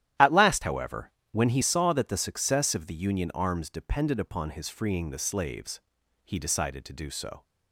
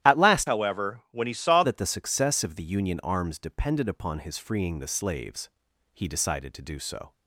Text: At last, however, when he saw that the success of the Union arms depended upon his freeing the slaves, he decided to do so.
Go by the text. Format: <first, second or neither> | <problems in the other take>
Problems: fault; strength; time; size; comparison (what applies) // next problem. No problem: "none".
first | starts louder than the rest; strong; until 1.1 s; 12.5 dB; strong in the first // changes voice from "however" to "saw"; from 0.4 to 1.6 s; 1.2 s long